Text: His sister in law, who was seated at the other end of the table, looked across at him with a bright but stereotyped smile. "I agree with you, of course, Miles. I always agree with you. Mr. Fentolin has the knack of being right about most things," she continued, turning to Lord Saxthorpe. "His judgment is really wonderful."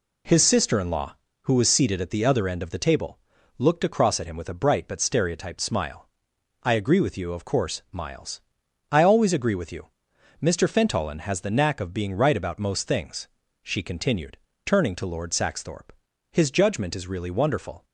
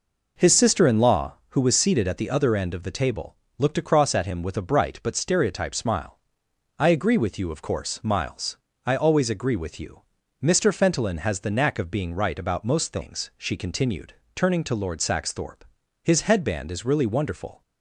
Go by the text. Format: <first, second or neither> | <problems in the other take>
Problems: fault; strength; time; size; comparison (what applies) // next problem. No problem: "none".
first | says "headband" for "judgment"; at 16.2 s